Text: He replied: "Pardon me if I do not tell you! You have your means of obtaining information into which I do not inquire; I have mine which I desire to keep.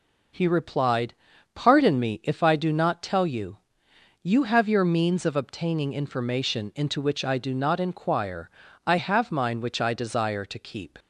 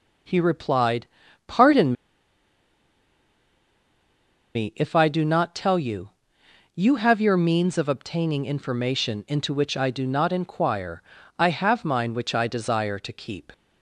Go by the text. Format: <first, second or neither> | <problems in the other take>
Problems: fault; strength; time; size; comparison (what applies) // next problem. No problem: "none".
first | pauses between "Pardon" and "me"; strong; at 1.9 s; 2.6 s long